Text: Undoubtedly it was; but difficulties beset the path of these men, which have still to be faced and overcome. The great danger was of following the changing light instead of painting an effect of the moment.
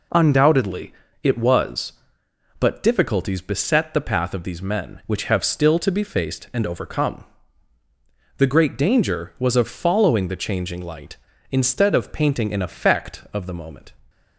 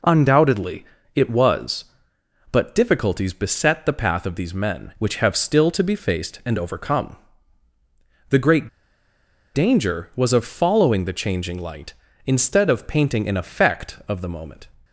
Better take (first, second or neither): first